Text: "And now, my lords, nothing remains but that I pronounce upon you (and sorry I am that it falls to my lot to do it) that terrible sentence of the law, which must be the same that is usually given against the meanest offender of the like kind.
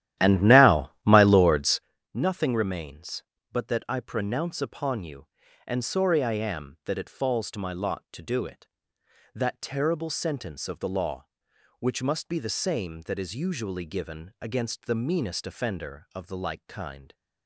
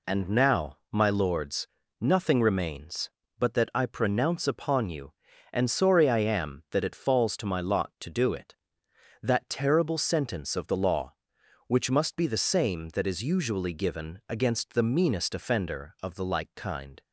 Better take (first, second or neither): second